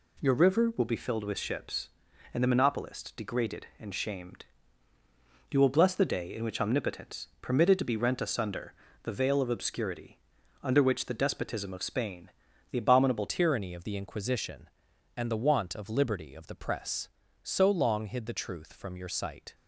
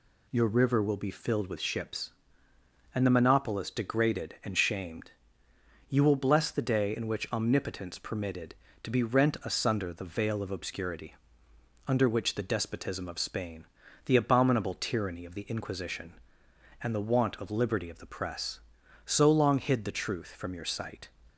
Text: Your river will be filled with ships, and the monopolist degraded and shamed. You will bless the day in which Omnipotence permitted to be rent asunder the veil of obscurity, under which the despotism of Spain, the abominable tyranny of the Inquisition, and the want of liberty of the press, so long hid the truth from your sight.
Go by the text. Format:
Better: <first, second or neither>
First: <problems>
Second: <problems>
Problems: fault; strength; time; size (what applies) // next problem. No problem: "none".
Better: second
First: pauses between "asunder" and "the"; slight; at 8.7 s; 0.30 s long // changes voice at "tyranny"; from 13.2 s on; 6.3 s long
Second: none